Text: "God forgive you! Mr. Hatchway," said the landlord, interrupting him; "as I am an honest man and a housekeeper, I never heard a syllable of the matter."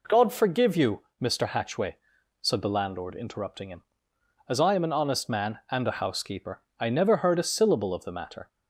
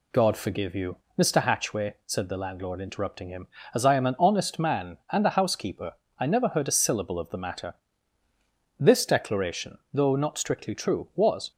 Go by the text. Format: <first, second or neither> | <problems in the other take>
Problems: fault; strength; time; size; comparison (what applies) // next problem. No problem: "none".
first | goes on to say "This declaration though not strictly true was"; strong; from 8.7 s on; 2.7 s long